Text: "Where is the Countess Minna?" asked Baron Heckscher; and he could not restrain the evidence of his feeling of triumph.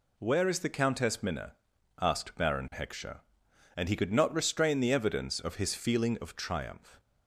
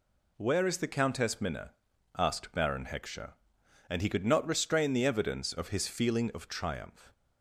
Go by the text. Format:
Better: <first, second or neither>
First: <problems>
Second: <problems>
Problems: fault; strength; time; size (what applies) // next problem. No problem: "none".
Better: neither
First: none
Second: none